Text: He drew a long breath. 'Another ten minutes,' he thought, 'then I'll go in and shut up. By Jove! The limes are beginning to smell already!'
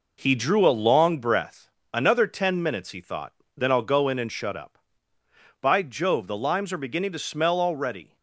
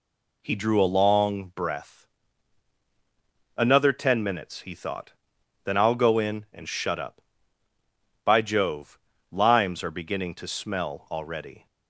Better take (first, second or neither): first